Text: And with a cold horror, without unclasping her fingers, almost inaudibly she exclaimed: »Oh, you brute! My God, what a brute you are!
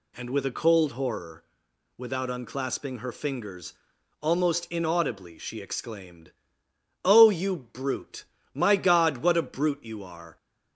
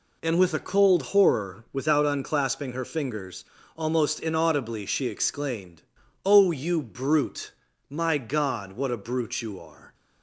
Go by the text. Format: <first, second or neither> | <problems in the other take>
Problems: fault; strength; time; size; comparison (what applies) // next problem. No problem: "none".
neither | none